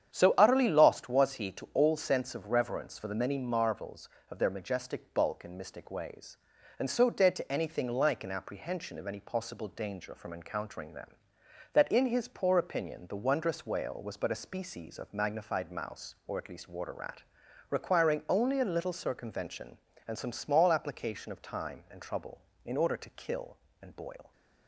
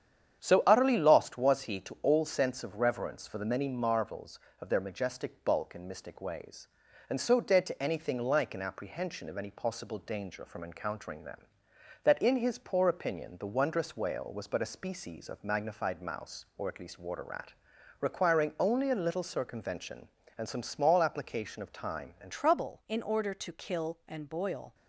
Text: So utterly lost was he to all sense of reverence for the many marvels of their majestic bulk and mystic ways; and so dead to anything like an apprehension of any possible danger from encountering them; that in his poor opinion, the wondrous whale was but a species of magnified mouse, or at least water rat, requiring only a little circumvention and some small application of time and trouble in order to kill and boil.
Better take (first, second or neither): first